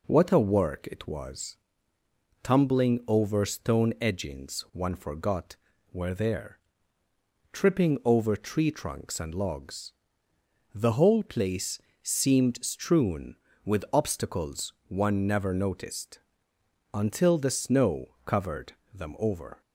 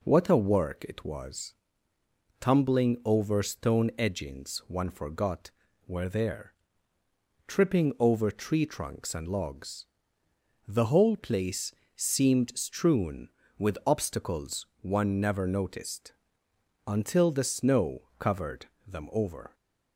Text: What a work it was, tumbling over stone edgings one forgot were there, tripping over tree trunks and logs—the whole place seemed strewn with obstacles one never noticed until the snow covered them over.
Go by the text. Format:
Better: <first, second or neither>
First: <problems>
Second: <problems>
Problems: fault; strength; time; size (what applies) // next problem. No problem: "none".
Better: neither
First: pauses between "place" and "seemed"; slight; at 11.8 s; 0.22 s long // pauses between "obstacles" and "one"; slight; at 14.7 s; 0.16 s long // pauses between "noticed" and "until"; noticeable; at 16.2 s; 0.74 s long // pauses between "covered" and "them"; slight; at 18.7 s; 0.20 s long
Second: pauses between "place" and "seemed"; slight; at 11.7 s; 0.22 s long // pauses between "obstacles" and "one"; slight; at 14.6 s; 0.16 s long // pauses between "noticed" and "until"; noticeable; at 16.1 s; 0.74 s long // pauses between "covered" and "them"; slight; at 18.6 s; 0.20 s long